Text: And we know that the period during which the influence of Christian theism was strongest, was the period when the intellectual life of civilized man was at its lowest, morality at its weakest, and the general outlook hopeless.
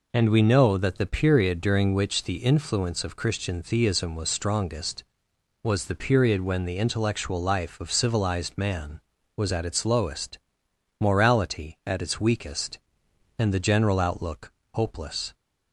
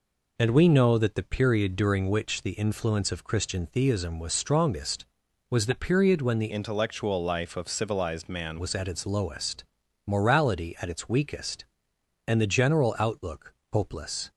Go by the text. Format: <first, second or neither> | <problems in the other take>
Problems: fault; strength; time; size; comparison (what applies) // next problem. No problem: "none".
first | changes voice from "intellectual" to "man"; from 6.4 to 8.5 s; 2.1 s long // pauses between "outlook" and "hopeless"; slight; at 13.5 s; 0.18 s long; slight in the first